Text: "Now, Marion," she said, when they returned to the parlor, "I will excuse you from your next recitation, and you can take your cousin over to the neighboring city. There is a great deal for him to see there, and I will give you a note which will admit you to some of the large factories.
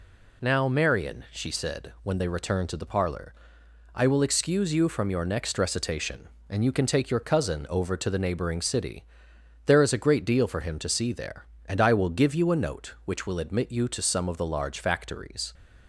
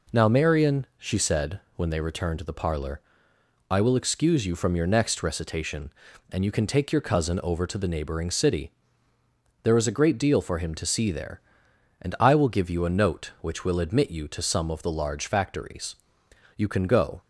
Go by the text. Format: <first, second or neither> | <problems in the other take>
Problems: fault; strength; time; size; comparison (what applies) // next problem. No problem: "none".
first | goes on to say "You can go"; noticeable; from 16.5 s on; 0.64 s long